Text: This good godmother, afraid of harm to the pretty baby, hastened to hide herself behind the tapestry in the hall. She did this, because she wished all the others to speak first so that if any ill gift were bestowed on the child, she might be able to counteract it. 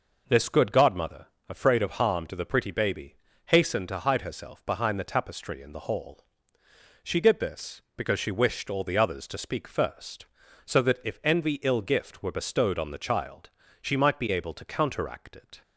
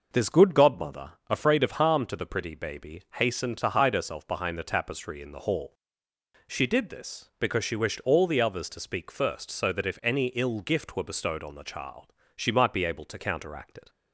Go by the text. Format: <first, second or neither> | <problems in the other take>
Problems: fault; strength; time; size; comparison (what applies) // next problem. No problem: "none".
second | says "envy" for "any"; at 11.2 s